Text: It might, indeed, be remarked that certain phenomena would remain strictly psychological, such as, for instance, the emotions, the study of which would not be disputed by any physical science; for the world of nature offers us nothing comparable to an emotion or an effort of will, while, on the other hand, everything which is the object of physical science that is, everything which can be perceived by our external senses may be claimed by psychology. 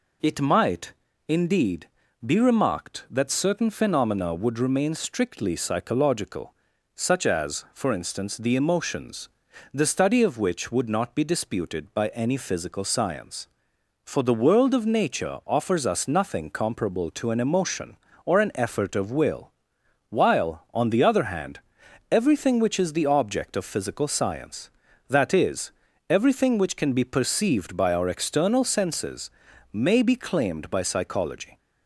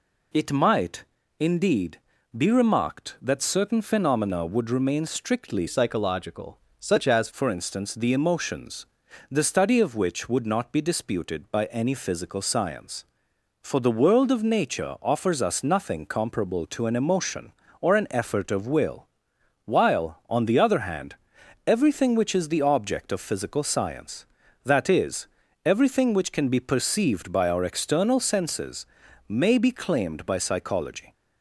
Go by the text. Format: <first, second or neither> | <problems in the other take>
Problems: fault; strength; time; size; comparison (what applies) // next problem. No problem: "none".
first | changes voice from "psychological" to "as"; from 5.6 to 7.2 s; 1.6 s long // pauses between "senses" and "may"; at 28.8 s; 0.44 s long; also in the first